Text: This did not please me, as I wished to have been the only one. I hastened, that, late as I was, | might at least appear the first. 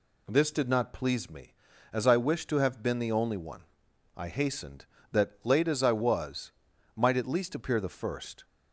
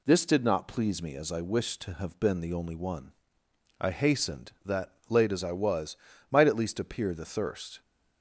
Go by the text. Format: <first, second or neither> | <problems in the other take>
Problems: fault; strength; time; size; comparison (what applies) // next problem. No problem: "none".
first | says "thirst" for "first"; at 7.2 s